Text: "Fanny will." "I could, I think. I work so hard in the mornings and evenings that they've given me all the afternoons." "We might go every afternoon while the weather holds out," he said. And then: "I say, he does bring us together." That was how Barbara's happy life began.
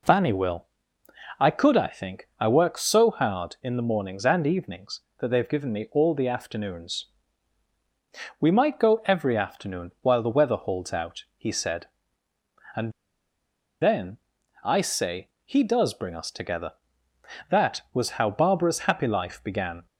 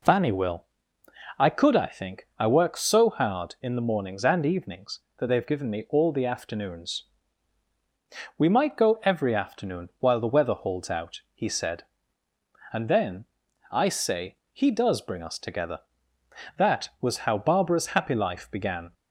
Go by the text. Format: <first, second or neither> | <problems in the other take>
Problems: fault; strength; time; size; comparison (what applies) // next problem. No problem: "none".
second | pauses between "And" and "then"; noticeable; at 12.9 s; 0.89 s long